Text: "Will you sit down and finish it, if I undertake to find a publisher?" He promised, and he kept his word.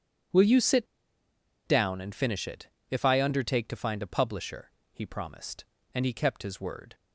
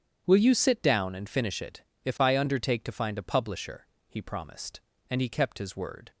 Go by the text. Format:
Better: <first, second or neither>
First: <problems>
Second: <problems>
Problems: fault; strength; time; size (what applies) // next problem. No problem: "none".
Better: second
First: starts louder than the rest; strong; until 2.1 s; 8.5 dB // pauses between "sit" and "down"; noticeable; at 0.8 s; 0.80 s long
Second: starts louder than the rest; strong; until 1.2 s; 8.5 dB